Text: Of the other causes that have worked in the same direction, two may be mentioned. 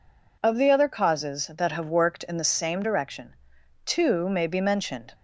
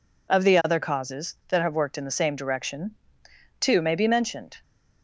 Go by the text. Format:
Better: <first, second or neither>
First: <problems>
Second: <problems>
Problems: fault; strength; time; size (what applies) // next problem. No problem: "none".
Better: neither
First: none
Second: none